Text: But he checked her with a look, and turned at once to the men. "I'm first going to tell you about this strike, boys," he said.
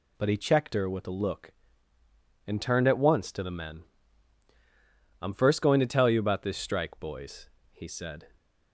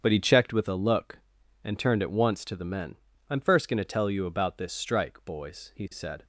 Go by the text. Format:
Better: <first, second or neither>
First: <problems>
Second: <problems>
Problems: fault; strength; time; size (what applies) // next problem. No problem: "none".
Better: first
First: none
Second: starts louder than the rest; strong; until 1.0 s; 7.5 dB // skips "her"; at 0.5 s